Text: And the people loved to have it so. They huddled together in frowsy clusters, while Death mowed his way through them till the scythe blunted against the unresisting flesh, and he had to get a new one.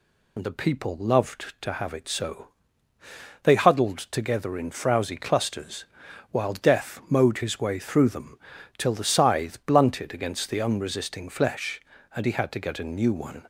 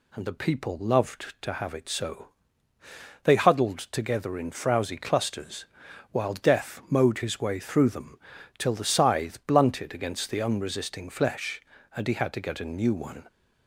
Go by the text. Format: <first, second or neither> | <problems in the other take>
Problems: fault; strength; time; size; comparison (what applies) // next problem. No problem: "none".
second | loses the start of "And"; at 0.3 s; 45 ms // pauses between "them" and "till"; at 8.3 s; 0.40 s long; also in the second